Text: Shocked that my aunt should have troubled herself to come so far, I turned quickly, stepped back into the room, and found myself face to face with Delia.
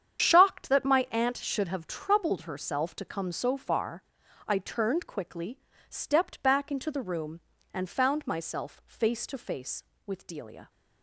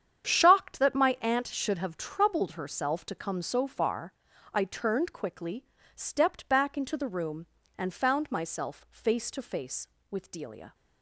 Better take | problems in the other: second | loses the start of "Shocked"; at 0.1 s; 50 ms // starts louder than the rest; strong; until 1.2 s; 8.5 dB; strong in the second

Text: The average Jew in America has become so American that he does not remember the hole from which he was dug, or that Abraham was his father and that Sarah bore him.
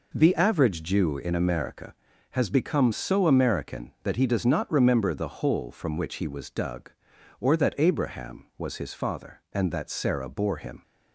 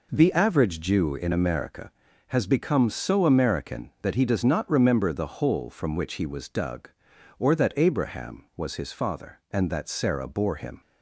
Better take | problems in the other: neither | none

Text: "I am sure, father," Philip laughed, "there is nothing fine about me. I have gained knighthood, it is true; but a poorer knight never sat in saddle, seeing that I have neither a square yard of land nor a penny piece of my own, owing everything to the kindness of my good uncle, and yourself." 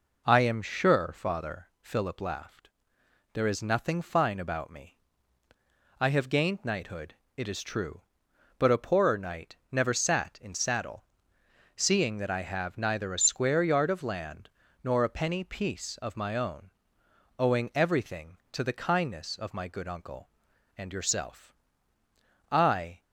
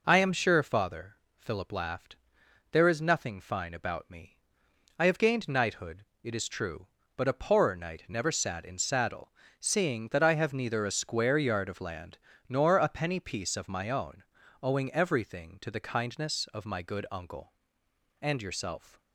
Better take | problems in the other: second | pauses between "land" and "nor"; slight; at 14.5 s; 0.32 s long; slight in the second // goes on to say "I"; from 22.5 s on; 0.50 s long

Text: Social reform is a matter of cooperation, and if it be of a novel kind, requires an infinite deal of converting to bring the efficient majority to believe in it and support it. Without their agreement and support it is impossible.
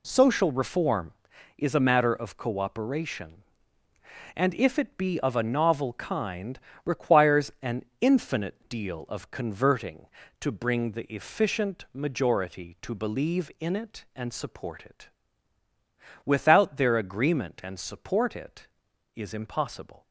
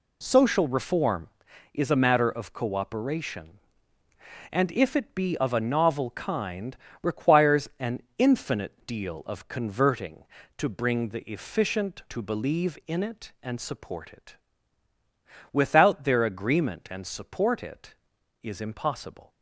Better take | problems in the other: first | pauses between "an" and "infinite"; slight; at 8.0 s; 0.16 s long; slight in the first // skips "majority"; at 12.0 s

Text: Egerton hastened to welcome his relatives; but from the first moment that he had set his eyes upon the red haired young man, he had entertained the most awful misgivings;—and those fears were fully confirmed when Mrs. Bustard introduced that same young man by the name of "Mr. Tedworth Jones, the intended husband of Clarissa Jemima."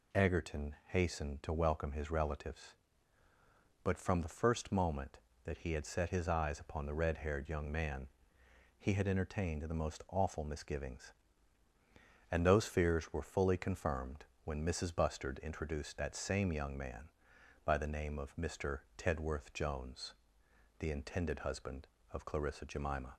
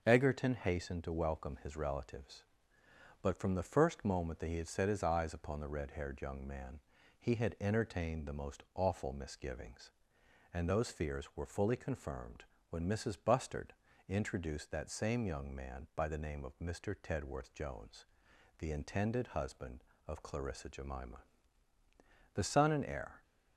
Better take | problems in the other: first | starts louder than the rest; until 1.0 s; 6.5 dB // pauses between "confirmed" and "when"; slight; at 12.4 s; 0.26 s long; slight in the first // pauses between "Bustard" and "introduced"; slight; at 13.7 s; 0.34 s long // goes on to say "The son and heir"; noticeable; from 22.3 s on; 0.88 s long

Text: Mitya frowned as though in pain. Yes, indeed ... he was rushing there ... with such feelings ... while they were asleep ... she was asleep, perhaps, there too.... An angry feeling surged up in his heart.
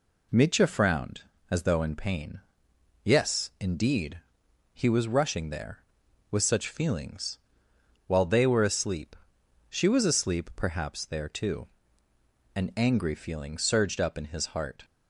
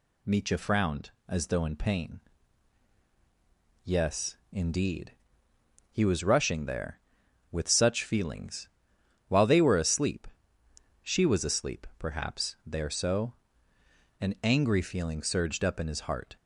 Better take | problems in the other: first | says "so" for "too"; at 12.9 s

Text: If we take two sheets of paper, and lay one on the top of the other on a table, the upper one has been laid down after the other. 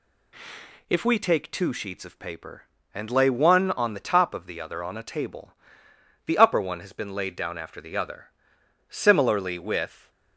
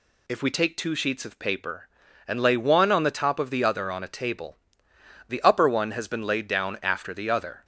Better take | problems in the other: second | goes on to say "Similarly with"; noticeable; from 8.8 s on; 1.2 s long

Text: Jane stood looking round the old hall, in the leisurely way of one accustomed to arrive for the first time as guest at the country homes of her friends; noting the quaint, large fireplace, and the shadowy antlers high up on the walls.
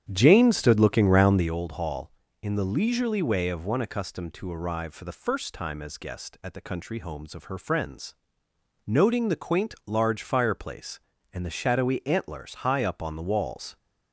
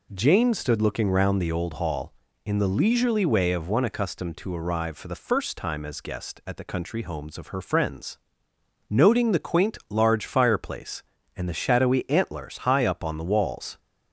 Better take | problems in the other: second | starts louder than the rest; strong; until 1.5 s; 9.5 dB

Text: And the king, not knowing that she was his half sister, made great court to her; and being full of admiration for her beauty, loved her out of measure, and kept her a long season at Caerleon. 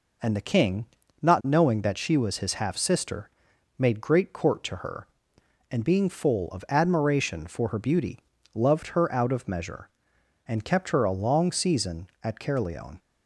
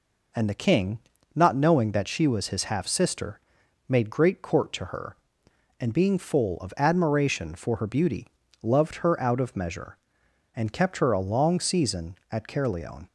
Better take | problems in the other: neither | none

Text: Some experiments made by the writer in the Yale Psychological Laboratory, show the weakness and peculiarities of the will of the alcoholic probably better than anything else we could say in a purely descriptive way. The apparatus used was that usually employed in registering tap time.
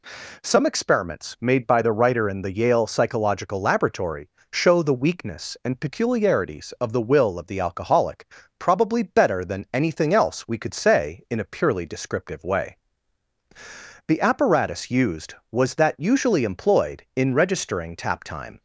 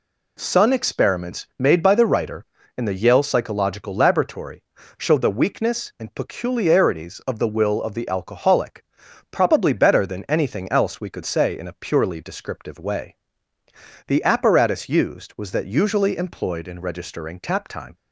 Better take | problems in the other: first | says "Sun" for "Some"; at 0.3 s // pauses between "alcoholic" and "probably"; noticeable; at 8.8 s; 0.46 s long; slight in the first

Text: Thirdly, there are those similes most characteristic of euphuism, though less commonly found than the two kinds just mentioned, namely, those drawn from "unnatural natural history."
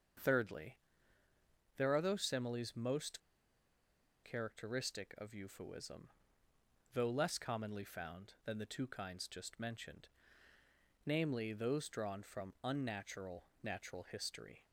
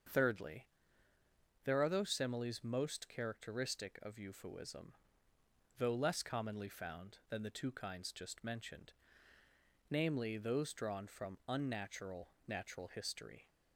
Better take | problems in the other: second | starts louder than the rest; until 2.2 s; 6.5 dB; also in the second // pauses between "most" and "characteristic"; at 3.1 s; 1.0 s long // pauses between "unnatural" and "natural"; slight; at 13.4 s; 0.16 s long; slight in the second

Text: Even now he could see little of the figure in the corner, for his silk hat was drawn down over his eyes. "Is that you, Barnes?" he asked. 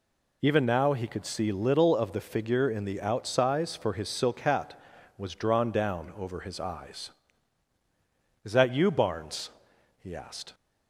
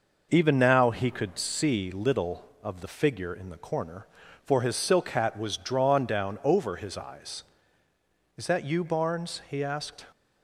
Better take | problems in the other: second | says "outsize" for "corner"; at 3.0 s

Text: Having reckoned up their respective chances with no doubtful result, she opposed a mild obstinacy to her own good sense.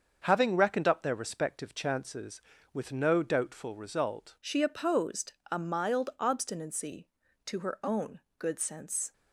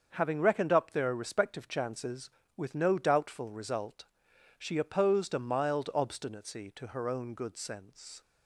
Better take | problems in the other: second | starts louder than the rest; until 1.2 s; 6.5 dB; also in the second // changes voice at "she"; from 4.3 s on; 4.8 s long // pauses between "opposed" and "a"; slight; at 5.3 s; 0.18 s long // pauses between "own" and "good"; slight; at 8.2 s; 0.18 s long

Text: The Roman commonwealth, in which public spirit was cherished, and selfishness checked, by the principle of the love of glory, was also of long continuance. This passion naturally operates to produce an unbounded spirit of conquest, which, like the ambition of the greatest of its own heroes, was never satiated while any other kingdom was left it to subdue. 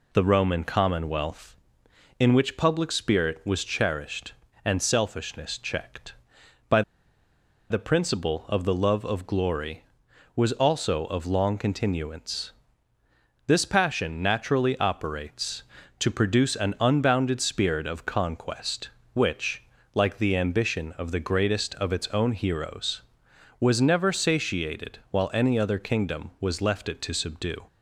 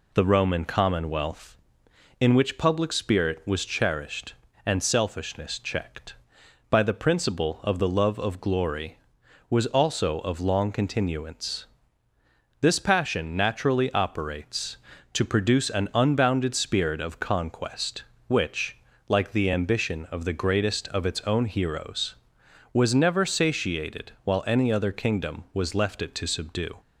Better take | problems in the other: second | pauses between "by" and "the"; noticeable; at 6.8 s; 0.88 s long

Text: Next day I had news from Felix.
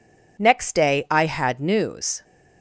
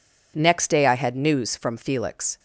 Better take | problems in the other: second | stops before "from Felix"; at 2.2 s

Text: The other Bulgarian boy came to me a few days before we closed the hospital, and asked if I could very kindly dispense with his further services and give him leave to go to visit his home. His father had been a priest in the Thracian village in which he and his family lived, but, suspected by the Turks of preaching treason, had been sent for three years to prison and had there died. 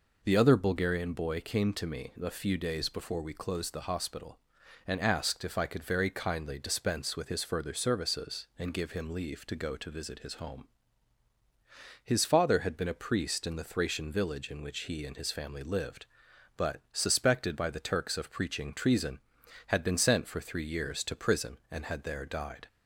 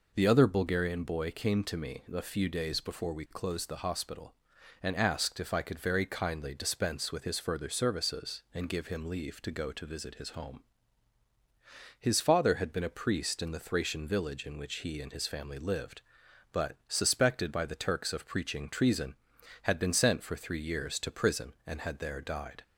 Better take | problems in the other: neither | none

